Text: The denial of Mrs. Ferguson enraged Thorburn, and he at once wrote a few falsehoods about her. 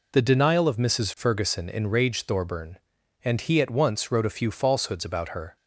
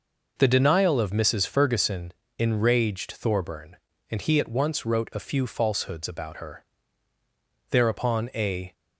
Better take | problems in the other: first | pauses between "Ferguson" and "enraged"; slight; at 2.1 s; 0.26 s long // goes on to say "Thereupon a"; noticeable; from 7.6 s on; 1.0 s long

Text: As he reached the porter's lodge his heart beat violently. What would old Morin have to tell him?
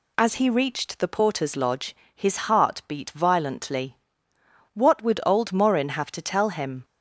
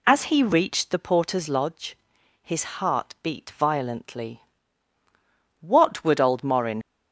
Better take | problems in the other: first | pauses between "lodge" and "his"; noticeable; at 1.9 s; 0.46 s long; slight in the first // stops before "have to tell him"; at 6.8 s

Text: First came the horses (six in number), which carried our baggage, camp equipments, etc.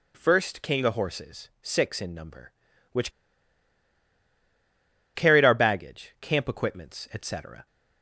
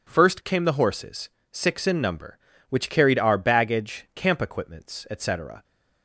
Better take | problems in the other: second | pauses between "which" and "carried"; strong; at 3.1 s; 2.0 s long

